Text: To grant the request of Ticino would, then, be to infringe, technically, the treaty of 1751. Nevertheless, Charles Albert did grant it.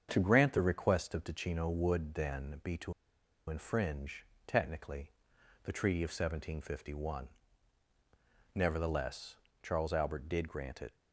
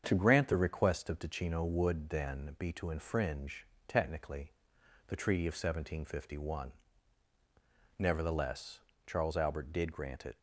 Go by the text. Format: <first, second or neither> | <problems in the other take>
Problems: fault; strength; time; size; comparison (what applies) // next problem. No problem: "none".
second | starts louder than the rest; strong; until 1.1 s; 7.5 dB; strong in the second // pauses between "to" and "infringe"; noticeable; at 2.9 s; 0.57 s long